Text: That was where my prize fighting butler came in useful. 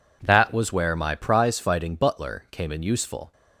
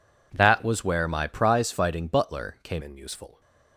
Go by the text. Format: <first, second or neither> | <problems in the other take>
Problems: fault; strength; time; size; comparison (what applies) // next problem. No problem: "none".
first | changes voice at "in"; from 2.8 s on; 0.6 s long